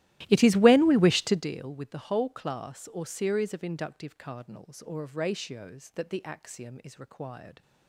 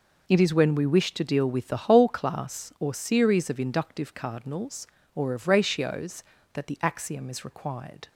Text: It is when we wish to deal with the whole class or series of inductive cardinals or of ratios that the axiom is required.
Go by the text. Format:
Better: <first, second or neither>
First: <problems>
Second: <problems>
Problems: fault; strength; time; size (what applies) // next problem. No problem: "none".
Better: second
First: starts louder than the rest; strong; until 1.5 s; 15.5 dB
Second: none